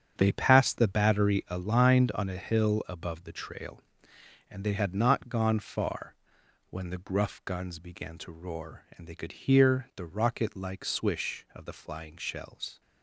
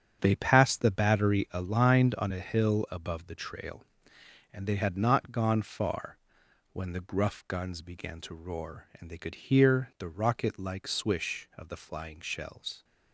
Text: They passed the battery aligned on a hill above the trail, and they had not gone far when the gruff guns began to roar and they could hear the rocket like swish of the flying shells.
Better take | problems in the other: neither | starts louder than the rest; strong; the same in both // pauses between "far" and "when"; noticeable; the same in both

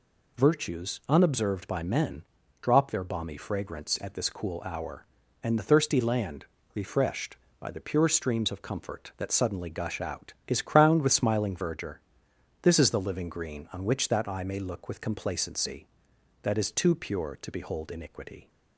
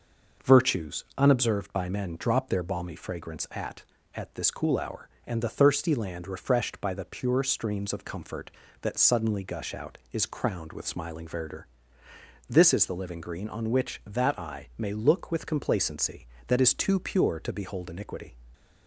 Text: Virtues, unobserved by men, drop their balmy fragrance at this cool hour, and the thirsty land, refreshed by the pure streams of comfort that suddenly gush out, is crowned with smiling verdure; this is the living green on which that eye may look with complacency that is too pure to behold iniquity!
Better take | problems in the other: first | says "at" twice; at 4.1 s

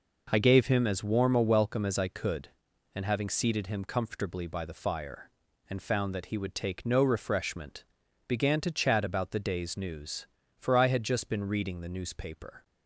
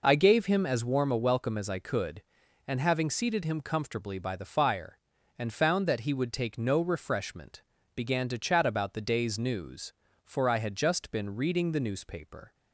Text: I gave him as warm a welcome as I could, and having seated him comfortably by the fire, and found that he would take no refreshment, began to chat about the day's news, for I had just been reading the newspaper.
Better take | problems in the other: neither | none

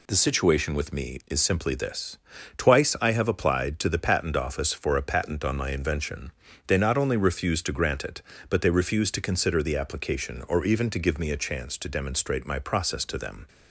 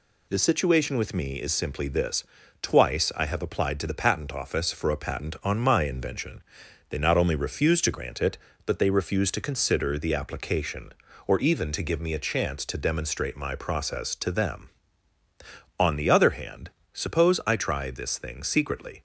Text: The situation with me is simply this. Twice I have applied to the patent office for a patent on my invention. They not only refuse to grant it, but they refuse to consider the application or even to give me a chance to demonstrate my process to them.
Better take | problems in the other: first | goes on to say "On the other hand suppose I try this thing secretly"; strong; from 15.7 s on; 3.2 s long

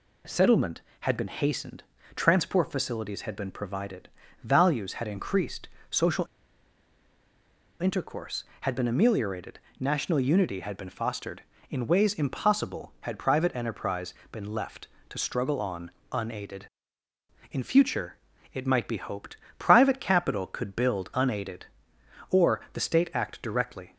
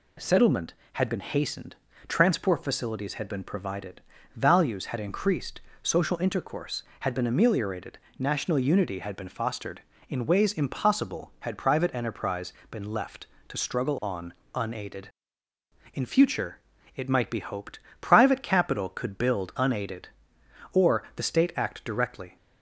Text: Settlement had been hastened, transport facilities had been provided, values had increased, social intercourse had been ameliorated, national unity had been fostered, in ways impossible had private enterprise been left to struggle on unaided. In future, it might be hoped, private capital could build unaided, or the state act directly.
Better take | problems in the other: second | pauses between "social" and "intercourse"; strong; at 6.2 s; 1.5 s long // pauses between "enterprise" and "been"; slight; at 14.1 s; 0.20 s long; slight in the second // pauses between "on" and "unaided"; slight; at 15.8 s; 0.22 s long; slight in the second

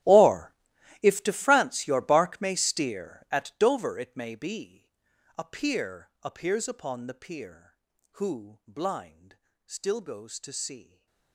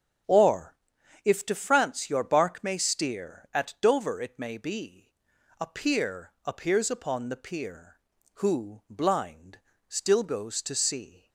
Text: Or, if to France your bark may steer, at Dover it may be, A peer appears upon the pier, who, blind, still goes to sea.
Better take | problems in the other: second | gets quieter; strong; throughout; 19.5 dB // starts louder than the rest; strong; until 1.5 s; 13.5 dB; strong in the second // stays silent after the last word; slight; from 10.8 s on; 0.5 s long

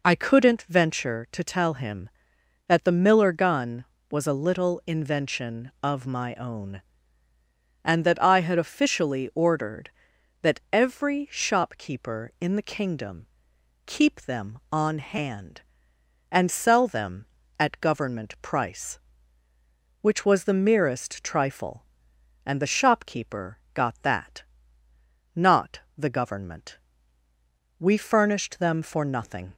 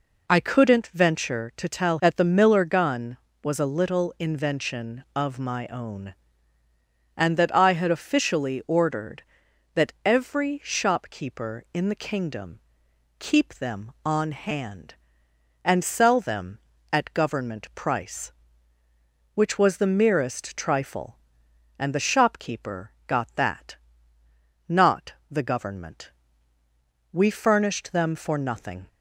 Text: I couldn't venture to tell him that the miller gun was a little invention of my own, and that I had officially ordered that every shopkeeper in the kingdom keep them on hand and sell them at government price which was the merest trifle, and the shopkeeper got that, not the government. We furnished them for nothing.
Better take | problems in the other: first | skips "him"; at 1.9 s // pauses between "kingdom" and "keep"; noticeable; at 12.5 s; 0.60 s long; noticeable in the first // pauses between "shopkeeper" and "got"; slight; at 22.9 s; 0.16 s long; slight in the first // pauses between "not" and "the"; slight; at 25.1 s; 0.16 s long; slight in the first

